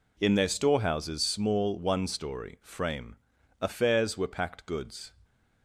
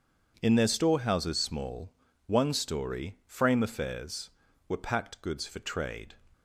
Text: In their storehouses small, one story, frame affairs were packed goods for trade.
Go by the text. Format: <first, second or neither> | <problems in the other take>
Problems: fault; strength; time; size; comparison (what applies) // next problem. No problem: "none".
second | pauses between "frame" and "affairs"; at 3.1 s; 0.42 s long // stops before "for trade"; at 5.2 s